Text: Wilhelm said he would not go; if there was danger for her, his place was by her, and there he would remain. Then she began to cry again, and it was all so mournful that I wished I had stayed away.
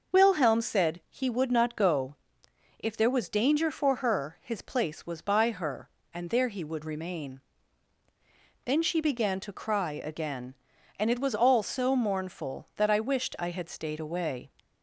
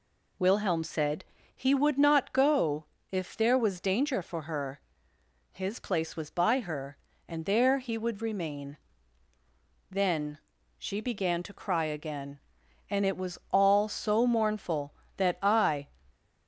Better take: first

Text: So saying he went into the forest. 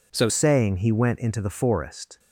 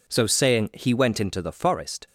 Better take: second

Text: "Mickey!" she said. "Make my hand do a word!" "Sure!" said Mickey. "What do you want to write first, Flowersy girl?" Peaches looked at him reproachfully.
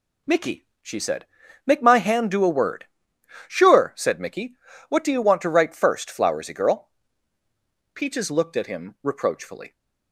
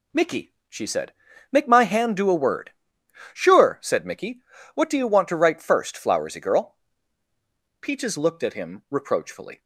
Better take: neither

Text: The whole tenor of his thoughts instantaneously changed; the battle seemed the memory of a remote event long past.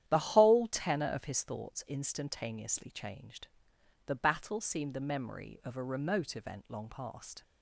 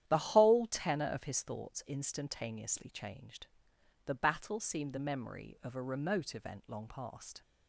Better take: neither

